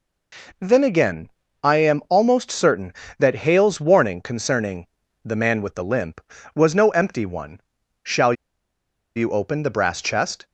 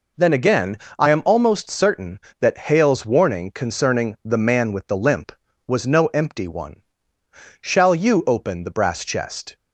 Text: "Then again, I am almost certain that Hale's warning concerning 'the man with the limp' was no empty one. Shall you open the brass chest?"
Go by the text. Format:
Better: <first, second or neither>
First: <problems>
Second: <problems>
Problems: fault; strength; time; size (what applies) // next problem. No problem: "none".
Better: second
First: pauses between "concerning" and "the"; slight; at 4.8 s; 0.36 s long // pauses between "Shall" and "you"; noticeable; at 8.3 s; 0.82 s long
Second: none